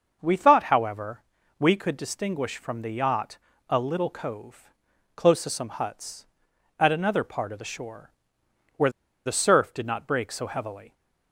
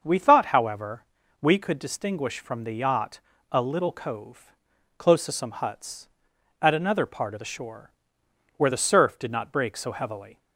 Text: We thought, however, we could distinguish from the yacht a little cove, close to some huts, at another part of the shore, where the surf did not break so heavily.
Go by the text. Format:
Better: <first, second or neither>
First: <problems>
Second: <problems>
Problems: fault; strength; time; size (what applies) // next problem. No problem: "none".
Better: second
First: starts louder than the rest; until 1.2 s; 6.5 dB // pauses between "yacht" and "a"; slight; at 3.3 s; 0.32 s long // pauses between "where" and "the"; at 8.8 s; 0.36 s long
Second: starts louder than the rest; until 1.0 s; 6.5 dB // pauses between "yacht" and "a"; slight; at 3.1 s; 0.32 s long